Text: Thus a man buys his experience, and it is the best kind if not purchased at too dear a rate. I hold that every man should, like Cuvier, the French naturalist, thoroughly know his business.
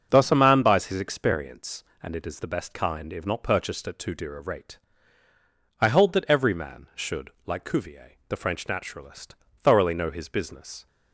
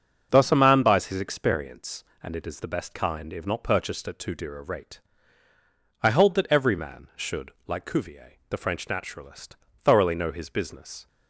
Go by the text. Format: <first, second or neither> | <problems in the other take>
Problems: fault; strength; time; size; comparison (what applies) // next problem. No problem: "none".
neither | starts louder than the rest; the same in both